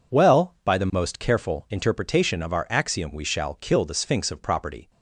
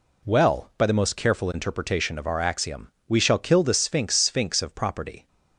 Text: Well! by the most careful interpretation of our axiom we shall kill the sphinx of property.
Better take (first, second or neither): first